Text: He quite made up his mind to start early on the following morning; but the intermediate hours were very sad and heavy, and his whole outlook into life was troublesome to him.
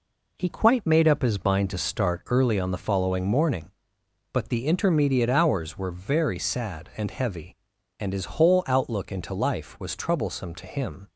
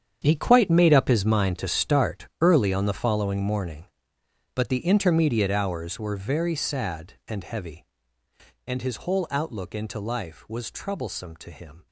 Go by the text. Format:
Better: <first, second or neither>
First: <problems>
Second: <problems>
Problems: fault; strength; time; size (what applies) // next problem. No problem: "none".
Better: first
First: none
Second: gets quieter; strong; throughout; 13.5 dB